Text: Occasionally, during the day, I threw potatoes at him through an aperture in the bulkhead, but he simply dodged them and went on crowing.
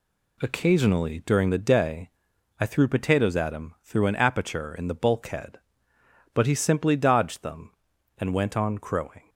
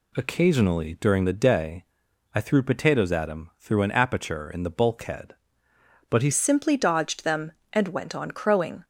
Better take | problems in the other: first | changes voice at "simply"; from 6.3 s on; 2.5 s long

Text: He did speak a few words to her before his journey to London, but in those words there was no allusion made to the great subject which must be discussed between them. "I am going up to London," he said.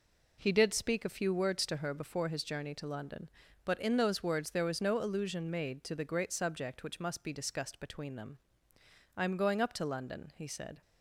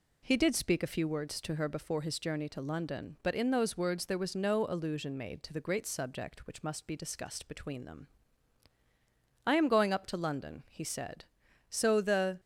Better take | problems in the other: first | goes on to say "So the"; noticeable; from 11.6 s on; 0.72 s long

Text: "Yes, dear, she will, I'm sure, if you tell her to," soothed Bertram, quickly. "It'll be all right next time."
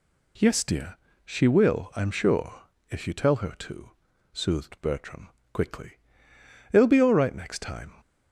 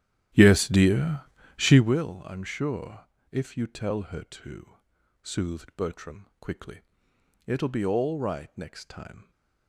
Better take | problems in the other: first | starts louder than the rest; strong; until 1.9 s; 12 dB

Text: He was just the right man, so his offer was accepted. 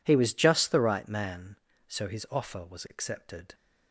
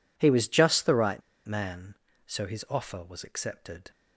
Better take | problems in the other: first | pauses between "right" and "man"; slight; at 1.2 s; 0.24 s long

